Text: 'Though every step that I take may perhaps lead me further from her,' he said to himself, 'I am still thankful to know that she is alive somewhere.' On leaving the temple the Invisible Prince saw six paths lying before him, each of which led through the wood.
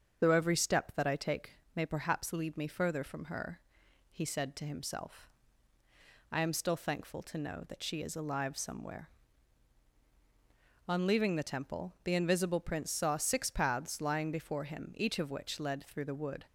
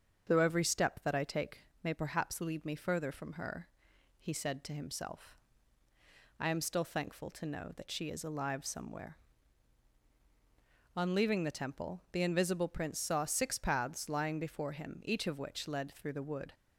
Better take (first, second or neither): second